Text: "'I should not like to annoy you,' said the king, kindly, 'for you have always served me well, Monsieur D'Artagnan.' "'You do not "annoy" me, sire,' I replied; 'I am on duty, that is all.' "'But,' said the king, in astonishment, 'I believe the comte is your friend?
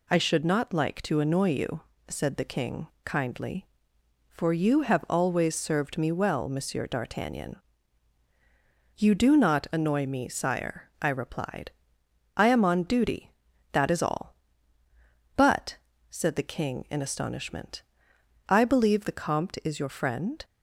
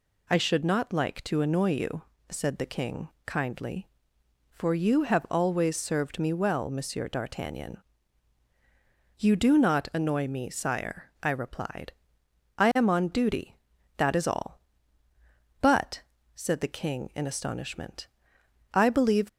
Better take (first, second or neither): first